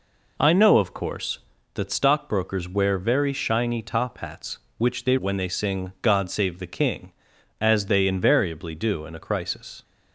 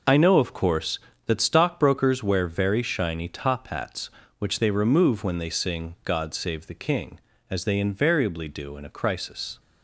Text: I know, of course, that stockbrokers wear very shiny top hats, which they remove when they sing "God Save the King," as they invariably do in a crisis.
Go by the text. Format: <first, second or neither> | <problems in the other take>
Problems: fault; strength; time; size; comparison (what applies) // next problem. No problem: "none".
second | skips "remove"; at 5.1 s